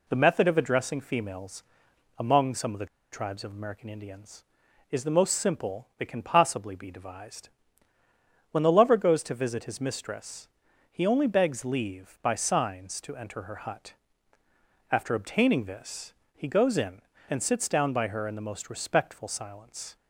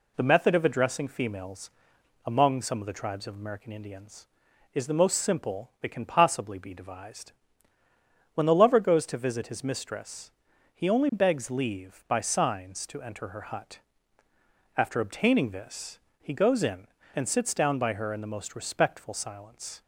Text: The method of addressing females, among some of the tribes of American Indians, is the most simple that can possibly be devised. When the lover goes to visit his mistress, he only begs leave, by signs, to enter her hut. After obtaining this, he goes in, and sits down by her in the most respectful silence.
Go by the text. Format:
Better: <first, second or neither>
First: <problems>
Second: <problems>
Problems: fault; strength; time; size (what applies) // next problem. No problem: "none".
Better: second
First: pauses between "the" and "tribes"; slight; at 2.8 s; 0.27 s long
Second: none